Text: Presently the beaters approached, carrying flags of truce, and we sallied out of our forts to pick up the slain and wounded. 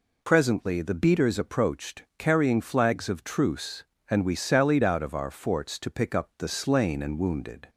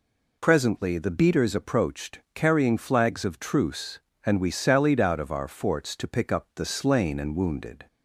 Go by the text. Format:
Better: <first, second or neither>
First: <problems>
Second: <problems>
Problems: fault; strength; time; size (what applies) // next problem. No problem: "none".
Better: neither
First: none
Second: none